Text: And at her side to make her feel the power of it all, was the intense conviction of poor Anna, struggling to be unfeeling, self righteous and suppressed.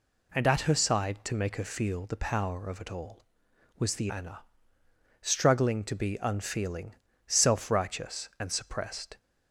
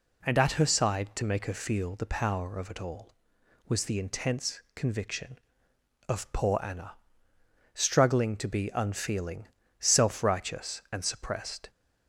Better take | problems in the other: second | skips "intense conviction of poor"; at 4.0 s

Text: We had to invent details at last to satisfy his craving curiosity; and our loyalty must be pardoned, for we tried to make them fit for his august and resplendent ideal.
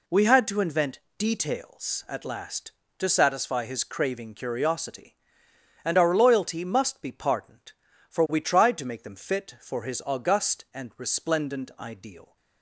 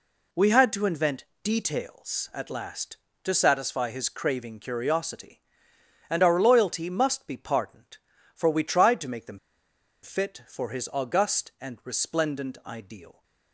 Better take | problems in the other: first | pauses between "invent" and "details"; slight; at 1.2 s; 0.18 s long; slight in the first // pauses between "them" and "fit"; noticeable; at 9.3 s; 0.63 s long

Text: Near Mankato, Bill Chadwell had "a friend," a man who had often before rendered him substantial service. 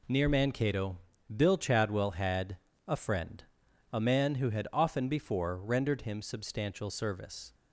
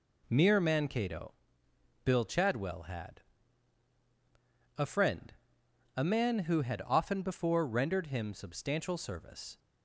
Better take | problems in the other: first | says "Mere" for "Near"; at 0.3 s // pauses between "had" and "a"; strong; at 3.2 s; 1.5 s long; slight in the first

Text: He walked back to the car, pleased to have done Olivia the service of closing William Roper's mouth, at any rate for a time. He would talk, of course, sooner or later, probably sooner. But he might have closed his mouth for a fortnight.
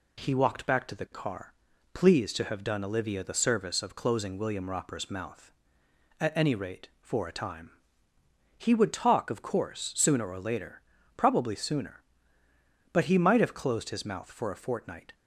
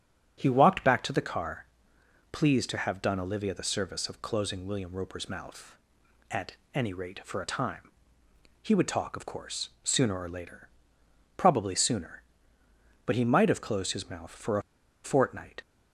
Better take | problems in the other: first | starts louder than the rest; strong; until 1.3 s; 10 dB // pauses between "at" and "any"; slight; at 6.5 s; 0.18 s long // pauses between "a" and "fortnight"; at 14.6 s; 0.42 s long

